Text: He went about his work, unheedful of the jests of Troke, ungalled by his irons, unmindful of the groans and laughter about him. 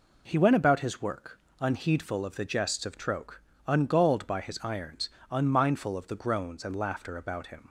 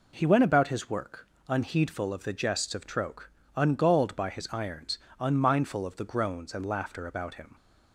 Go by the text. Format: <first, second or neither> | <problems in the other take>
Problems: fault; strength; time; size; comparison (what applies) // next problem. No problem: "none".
neither | none